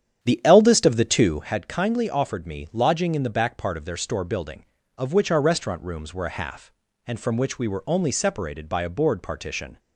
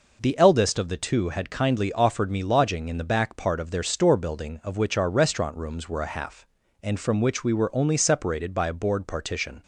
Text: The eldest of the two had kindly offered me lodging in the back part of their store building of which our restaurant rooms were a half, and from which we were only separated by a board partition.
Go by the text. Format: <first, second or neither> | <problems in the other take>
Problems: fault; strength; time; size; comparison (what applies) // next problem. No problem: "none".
second | starts louder than the rest; strong; until 1.5 s; 9 dB